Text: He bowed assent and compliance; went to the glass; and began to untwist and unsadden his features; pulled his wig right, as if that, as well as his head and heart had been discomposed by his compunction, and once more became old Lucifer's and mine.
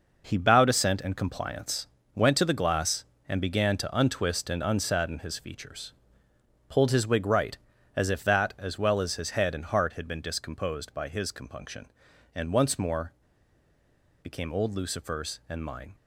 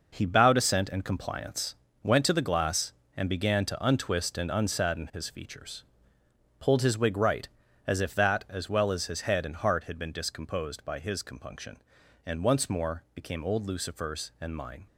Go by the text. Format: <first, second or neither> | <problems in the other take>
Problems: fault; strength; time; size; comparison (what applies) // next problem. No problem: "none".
second | pauses between "more" and "became"; at 13.1 s; 1.1 s long